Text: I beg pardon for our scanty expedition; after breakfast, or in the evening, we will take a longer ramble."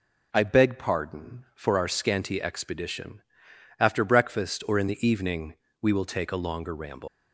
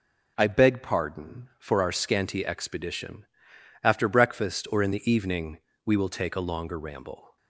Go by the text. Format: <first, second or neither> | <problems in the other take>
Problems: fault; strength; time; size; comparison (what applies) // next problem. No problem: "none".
second | leaves "ramble" unfinished; at 7.0 s; 245 ms